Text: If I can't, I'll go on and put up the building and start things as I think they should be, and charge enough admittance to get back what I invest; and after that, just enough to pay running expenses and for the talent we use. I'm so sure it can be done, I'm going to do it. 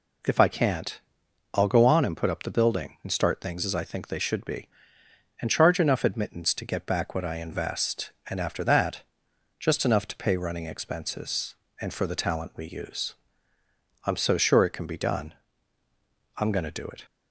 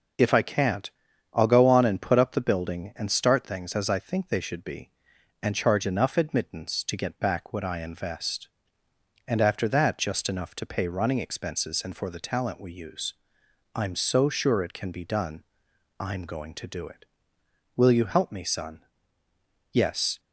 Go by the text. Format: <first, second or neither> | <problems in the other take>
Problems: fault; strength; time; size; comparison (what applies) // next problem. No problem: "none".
first | goes on to say "Will you help me son Yes"; strong; from 17.7 s on; 2.4 s long